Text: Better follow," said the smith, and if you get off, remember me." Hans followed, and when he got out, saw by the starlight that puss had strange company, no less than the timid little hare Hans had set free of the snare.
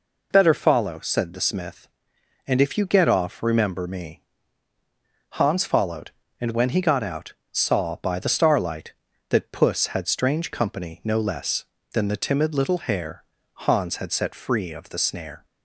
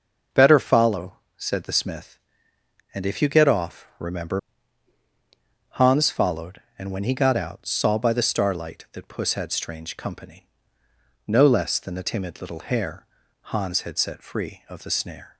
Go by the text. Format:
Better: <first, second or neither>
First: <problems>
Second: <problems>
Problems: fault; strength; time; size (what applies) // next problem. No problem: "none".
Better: first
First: pauses between "hare" and "Hans"; slight; at 13.2 s; 0.30 s long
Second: skips "me"; at 5.0 s // pauses between "hare" and "Hans"; slight; at 13.0 s; 0.36 s long